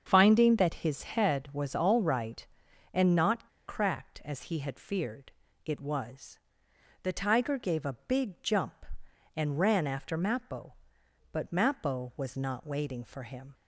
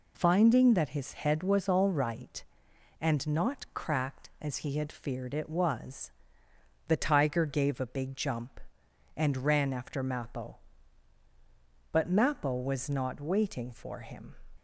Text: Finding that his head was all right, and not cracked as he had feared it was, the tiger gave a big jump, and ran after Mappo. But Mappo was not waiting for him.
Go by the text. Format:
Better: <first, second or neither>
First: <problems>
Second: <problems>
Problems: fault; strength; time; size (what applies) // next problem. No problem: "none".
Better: second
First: starts louder than the rest; until 1.0 s; 7 dB // pauses between "not" and "cracked"; slight; at 3.4 s; 0.19 s long // pauses between "feared" and "it"; slight; at 5.2 s; 0.34 s long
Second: none